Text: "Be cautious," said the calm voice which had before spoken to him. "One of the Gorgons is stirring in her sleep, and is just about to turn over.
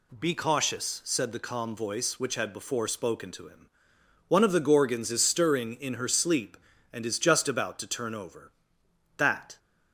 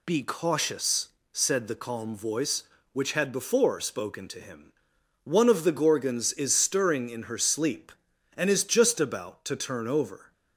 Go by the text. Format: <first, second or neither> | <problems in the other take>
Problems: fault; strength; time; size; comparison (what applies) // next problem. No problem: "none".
second | goes on to say "That"; slight; from 9.1 s on; 0.40 s long